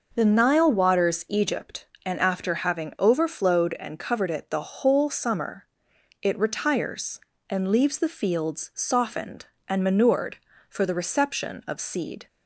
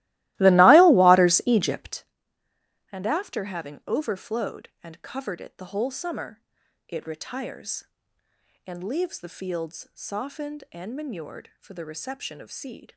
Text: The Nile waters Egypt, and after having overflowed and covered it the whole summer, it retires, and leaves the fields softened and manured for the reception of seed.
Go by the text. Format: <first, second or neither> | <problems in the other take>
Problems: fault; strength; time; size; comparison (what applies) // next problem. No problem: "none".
first | starts louder than the rest; strong; until 2.2 s; 18 dB